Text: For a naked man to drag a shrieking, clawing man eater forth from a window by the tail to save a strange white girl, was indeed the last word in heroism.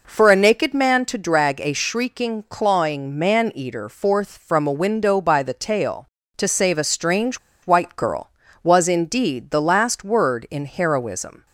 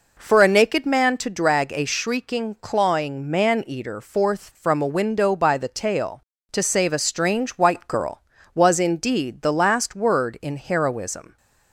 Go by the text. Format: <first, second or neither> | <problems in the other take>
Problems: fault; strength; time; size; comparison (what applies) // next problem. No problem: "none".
second | pauses between "strange" and "white"; slight; at 7.3 s; 0.26 s long